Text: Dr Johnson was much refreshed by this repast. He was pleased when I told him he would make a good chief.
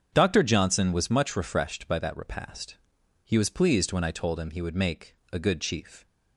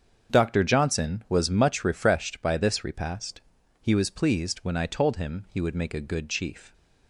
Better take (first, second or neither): second